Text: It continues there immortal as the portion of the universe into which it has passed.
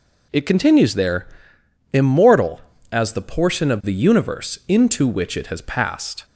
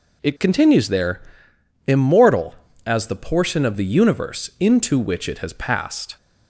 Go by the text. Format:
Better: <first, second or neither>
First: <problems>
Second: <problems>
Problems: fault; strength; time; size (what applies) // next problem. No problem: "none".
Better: neither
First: pauses between "there" and "immortal"; noticeable; at 1.2 s; 0.66 s long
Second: pauses between "there" and "immortal"; noticeable; at 1.2 s; 0.66 s long